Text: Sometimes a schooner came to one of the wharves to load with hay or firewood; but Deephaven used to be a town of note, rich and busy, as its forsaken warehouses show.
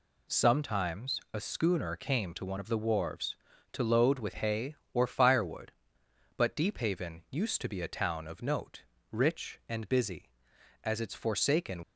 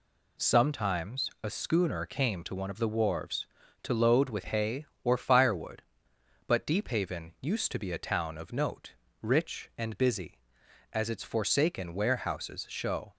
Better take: second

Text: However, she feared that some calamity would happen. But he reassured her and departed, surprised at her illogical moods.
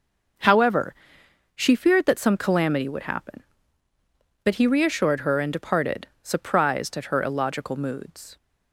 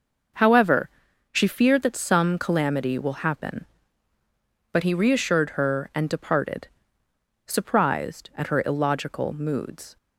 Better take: first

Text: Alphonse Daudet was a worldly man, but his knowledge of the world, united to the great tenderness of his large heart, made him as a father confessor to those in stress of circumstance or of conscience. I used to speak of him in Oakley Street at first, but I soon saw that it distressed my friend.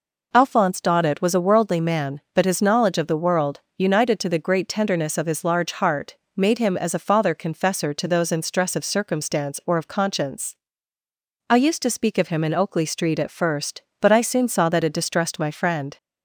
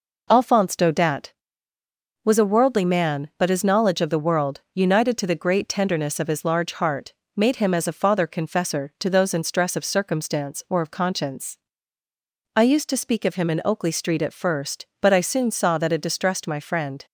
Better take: neither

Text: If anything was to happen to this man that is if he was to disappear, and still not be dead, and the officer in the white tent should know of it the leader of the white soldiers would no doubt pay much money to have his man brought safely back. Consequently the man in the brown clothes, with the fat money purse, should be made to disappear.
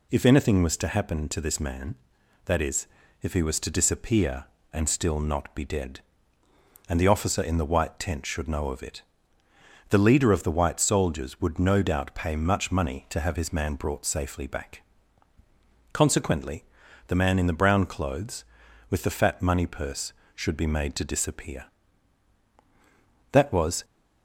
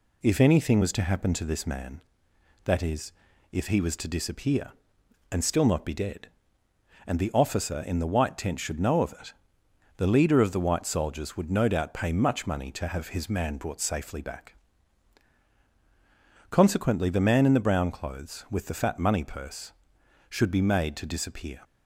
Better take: second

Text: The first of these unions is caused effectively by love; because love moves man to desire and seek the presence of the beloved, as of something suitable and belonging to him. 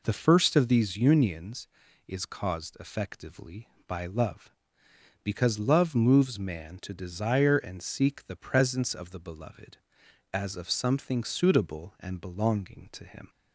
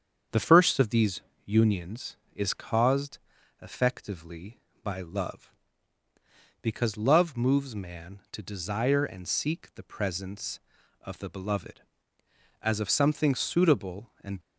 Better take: first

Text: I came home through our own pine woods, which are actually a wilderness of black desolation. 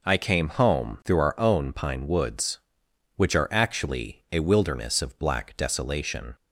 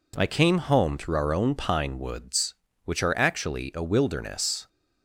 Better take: first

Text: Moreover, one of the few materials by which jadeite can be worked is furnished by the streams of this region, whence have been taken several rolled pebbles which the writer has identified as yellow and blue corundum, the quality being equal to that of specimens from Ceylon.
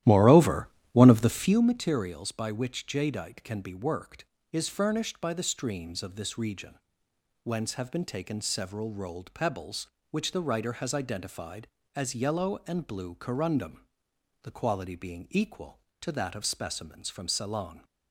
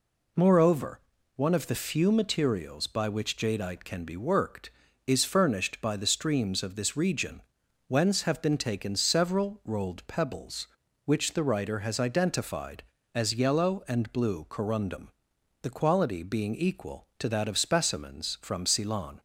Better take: second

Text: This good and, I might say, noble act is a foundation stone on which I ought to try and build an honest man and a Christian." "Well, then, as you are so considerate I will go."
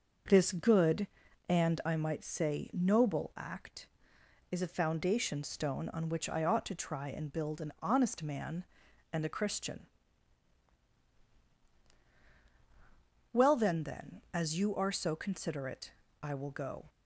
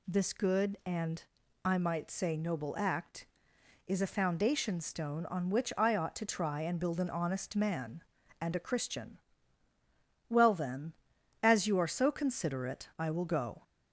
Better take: second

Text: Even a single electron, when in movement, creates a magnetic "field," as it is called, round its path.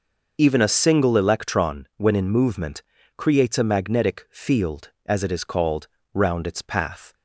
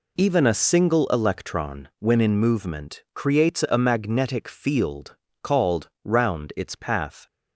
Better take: first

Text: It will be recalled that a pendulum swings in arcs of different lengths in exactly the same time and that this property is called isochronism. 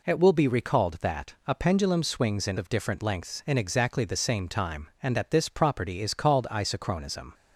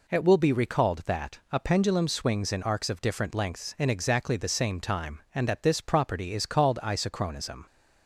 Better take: second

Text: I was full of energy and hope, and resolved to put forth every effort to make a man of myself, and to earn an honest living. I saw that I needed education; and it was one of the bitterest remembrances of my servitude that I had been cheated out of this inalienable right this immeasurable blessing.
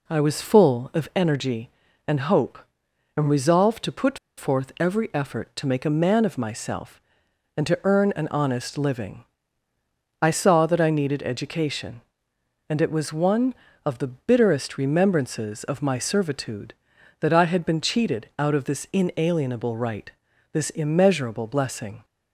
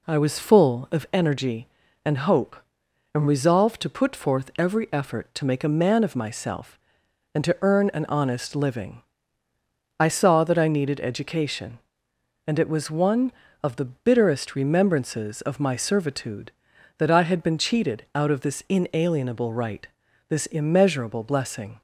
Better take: second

